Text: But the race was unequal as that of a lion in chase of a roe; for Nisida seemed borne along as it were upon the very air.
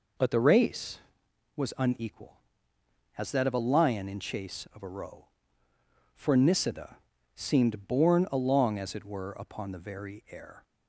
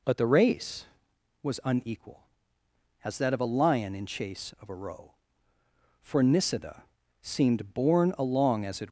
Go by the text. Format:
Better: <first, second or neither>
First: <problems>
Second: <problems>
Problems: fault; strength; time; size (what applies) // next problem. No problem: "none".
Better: first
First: pauses between "Nisida" and "seemed"; at 6.9 s; 0.38 s long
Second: pauses between "Nisida" and "seemed"; at 6.8 s; 0.38 s long // stops before "were upon the very air"; at 8.8 s